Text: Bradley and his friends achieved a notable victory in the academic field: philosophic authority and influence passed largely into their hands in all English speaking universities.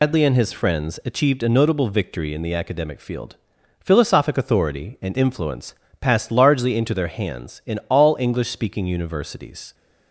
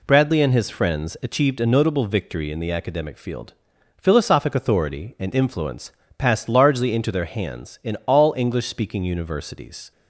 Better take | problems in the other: second | loses the start of "Bradley"; at 0.0 s; 155 ms // pauses between "influence" and "passed"; slight; at 5.7 s; 0.24 s long; slight in the second

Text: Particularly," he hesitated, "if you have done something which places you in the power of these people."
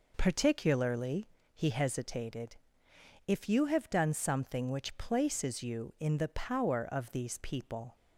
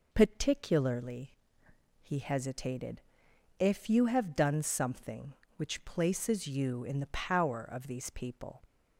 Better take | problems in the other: neither | none

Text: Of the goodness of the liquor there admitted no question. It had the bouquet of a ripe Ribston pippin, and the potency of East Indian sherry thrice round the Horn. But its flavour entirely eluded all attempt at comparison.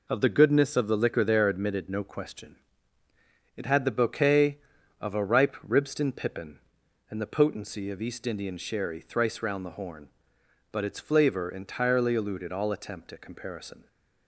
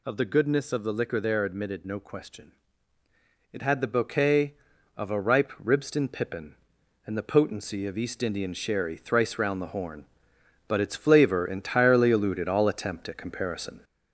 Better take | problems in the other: first | gets louder; noticeable; throughout; 4 dB

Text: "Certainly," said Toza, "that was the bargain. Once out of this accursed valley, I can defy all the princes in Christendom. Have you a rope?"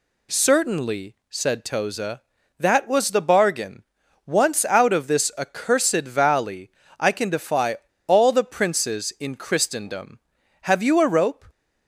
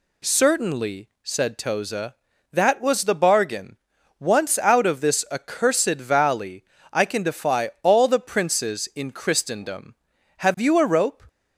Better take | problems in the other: second | pauses between "defy" and "all"; slight; at 7.7 s; 0.30 s long

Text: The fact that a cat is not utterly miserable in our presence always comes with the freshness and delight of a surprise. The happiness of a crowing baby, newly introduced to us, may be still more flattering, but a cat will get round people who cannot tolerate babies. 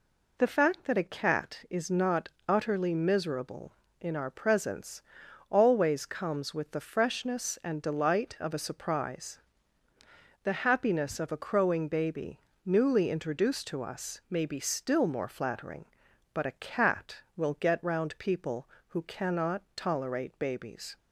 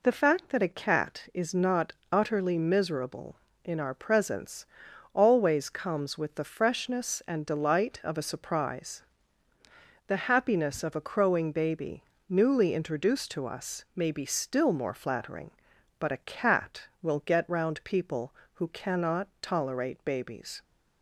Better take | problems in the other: neither | pauses between "not" and "utterly"; slight; the same in both // pauses between "presence" and "always"; noticeable; the same in both // pauses between "cannot" and "tolerate"; slight; the same in both

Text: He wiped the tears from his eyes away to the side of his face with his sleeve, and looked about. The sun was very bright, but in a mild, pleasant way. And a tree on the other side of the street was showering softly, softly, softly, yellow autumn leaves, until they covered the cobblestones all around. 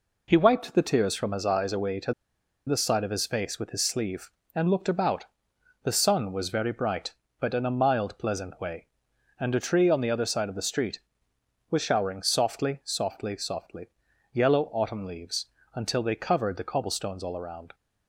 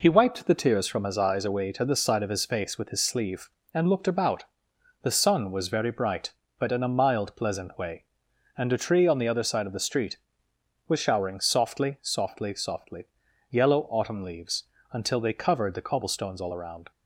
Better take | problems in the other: second | pauses between "to" and "the"; noticeable; at 2.1 s; 0.53 s long

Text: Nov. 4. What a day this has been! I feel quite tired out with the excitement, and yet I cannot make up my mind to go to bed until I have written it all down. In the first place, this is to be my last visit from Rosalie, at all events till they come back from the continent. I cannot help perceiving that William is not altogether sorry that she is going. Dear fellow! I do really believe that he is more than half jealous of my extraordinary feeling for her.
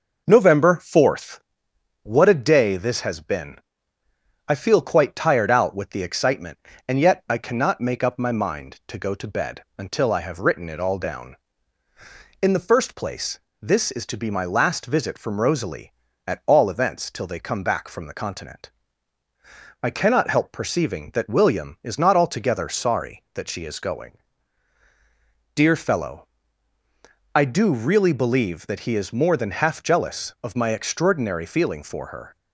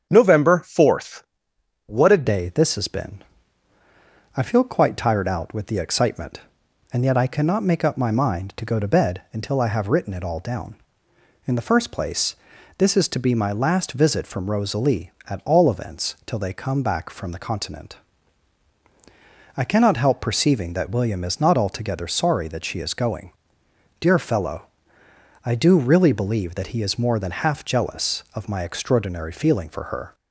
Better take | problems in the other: first | starts louder than the rest; strong; until 1.1 s; 8 dB // changes voice at "day"; from 2.2 s on; 27.9 s long

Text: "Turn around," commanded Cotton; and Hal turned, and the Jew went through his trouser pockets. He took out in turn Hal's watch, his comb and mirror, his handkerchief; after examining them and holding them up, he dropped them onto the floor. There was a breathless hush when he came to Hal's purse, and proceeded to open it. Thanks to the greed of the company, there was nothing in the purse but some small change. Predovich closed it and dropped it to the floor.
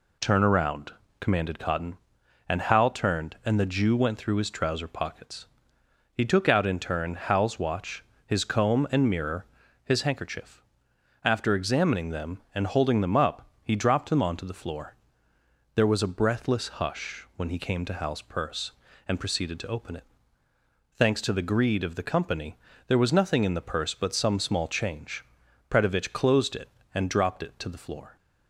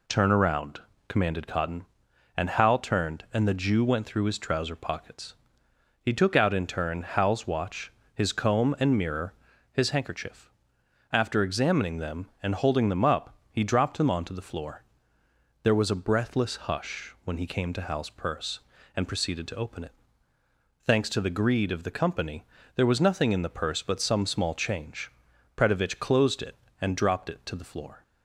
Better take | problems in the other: neither | none

